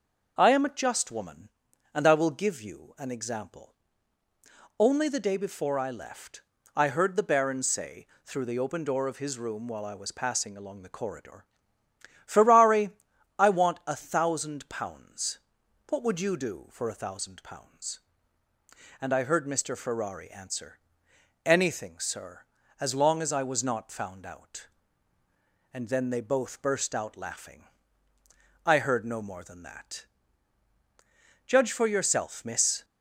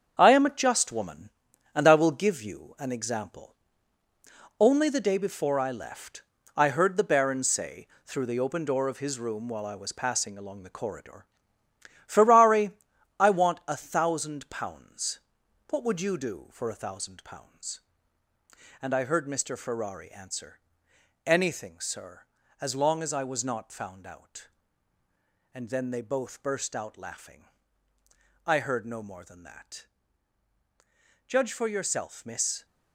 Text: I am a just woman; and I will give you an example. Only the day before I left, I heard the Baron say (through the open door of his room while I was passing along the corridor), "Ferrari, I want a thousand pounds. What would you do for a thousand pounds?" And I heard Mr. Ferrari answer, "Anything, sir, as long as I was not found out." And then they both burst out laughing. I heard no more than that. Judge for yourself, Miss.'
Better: first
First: none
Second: gets quieter; strong; throughout; 8 dB

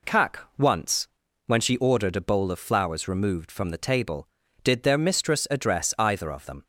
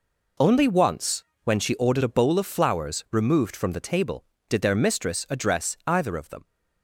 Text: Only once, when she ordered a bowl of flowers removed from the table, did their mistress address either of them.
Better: second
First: says "Kak" for "Only"; at 0.0 s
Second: none

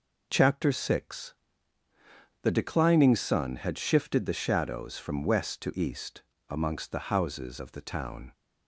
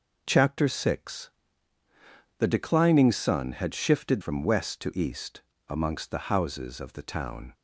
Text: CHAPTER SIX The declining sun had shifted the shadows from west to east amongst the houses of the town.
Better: first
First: pauses between "SIX" and "The"; at 1.3 s; 1.1 s long // pauses between "east" and "amongst"; slight; at 6.2 s; 0.30 s long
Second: pauses between "SIX" and "The"; at 1.2 s; 1.1 s long // skips "the shadows"; at 4.2 s // pauses between "east" and "amongst"; slight; at 5.3 s; 0.30 s long

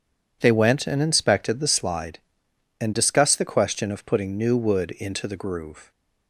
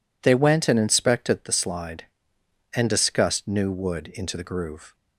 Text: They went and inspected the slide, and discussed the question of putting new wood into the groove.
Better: first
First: none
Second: skips "the question of putting"; at 3.4 s

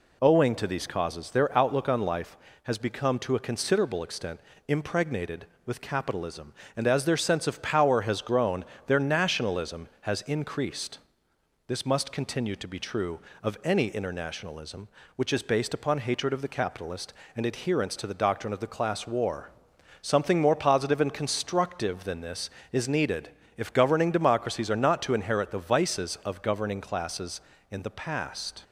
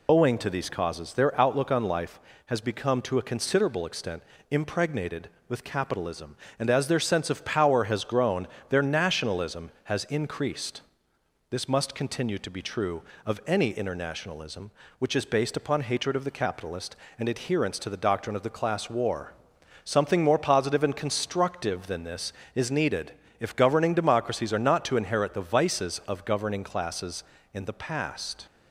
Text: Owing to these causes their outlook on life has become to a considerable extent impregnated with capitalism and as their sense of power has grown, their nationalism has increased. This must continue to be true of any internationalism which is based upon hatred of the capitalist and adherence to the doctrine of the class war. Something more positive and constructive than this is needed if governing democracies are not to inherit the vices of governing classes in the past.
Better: first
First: pauses between "extent" and "impregnated"; slight; at 4.4 s; 0.26 s long // pauses between "needed" and "if"; slight; at 23.2 s; 0.28 s long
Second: loses the start of "Owing"; at 0.0 s; 55 ms // pauses between "extent" and "impregnated"; slight; at 4.2 s; 0.26 s long // pauses between "needed" and "if"; slight; at 23.1 s; 0.28 s long

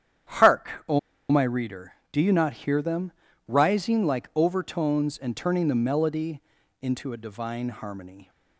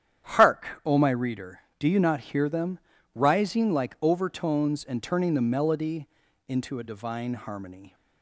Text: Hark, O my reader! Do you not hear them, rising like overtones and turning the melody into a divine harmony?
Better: second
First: starts louder than the rest; strong; until 1.6 s; 9.5 dB // pauses between "O" and "my"; slight; at 0.9 s; 0.30 s long // pauses between "melody" and "into"; at 6.4 s; 0.40 s long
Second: starts louder than the rest; strong; until 1.3 s; 9.5 dB // pauses between "melody" and "into"; at 6.0 s; 0.40 s long

